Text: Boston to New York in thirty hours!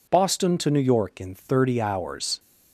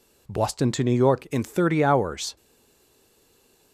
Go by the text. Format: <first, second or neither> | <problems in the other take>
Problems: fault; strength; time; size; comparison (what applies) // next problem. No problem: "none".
first | stays silent after the last word; noticeable; from 2.3 s on; 1.4 s long